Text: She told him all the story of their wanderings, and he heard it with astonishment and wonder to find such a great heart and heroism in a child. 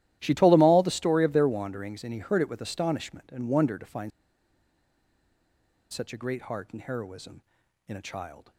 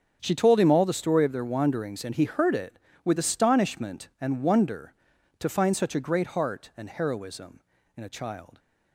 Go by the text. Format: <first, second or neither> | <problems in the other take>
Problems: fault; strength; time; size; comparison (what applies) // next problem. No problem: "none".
second | starts louder than the rest; strong; until 1.2 s; 13.5 dB; also in the second // pauses between "find" and "such"; strong; at 4.1 s; 1.8 s long